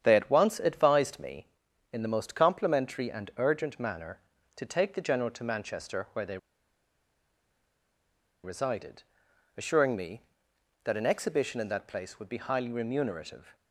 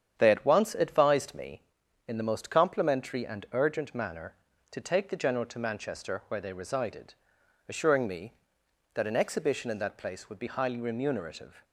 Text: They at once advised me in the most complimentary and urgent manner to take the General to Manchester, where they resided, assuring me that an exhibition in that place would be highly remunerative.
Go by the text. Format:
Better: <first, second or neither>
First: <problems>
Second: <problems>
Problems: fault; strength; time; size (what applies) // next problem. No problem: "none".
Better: second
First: starts louder than the rest; strong; until 1.0 s; 9 dB // pauses between "they" and "resided"; strong; at 6.3 s; 2.0 s long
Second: starts louder than the rest; strong; until 1.2 s; 9 dB